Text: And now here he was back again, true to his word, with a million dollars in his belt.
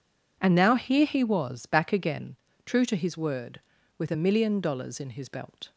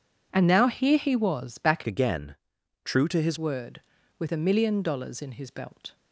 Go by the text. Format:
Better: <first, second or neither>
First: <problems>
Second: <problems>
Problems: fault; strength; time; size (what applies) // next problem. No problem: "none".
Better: first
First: none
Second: changes voice from "again" to "his"; from 1.8 to 3.3 s; 1.5 s long